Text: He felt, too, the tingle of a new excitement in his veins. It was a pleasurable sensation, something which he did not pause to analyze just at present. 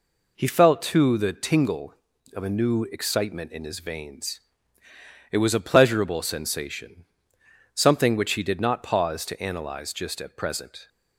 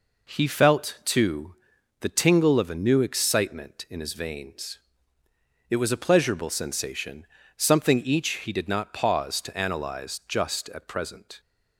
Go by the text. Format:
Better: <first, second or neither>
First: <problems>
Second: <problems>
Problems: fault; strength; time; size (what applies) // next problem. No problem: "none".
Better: first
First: none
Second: says "each" for "which"; at 7.9 s